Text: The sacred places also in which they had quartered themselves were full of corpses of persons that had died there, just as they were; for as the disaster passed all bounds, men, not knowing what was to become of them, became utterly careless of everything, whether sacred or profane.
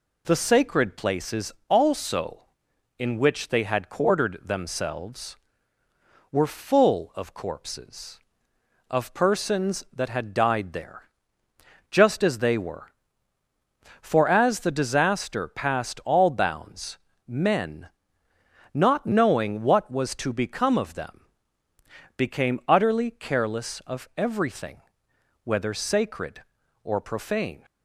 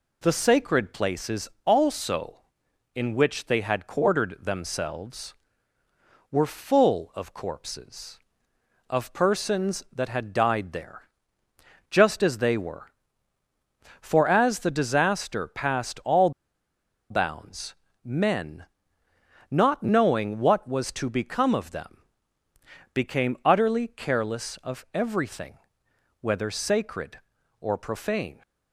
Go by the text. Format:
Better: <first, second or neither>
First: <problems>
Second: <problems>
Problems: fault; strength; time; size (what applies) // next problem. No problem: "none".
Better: first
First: pauses between "places" and "also"; slight; at 1.5 s; 0.16 s long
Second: pauses between "places" and "also"; slight; at 1.4 s; 0.16 s long // pauses between "all" and "bounds"; noticeable; at 16.3 s; 0.79 s long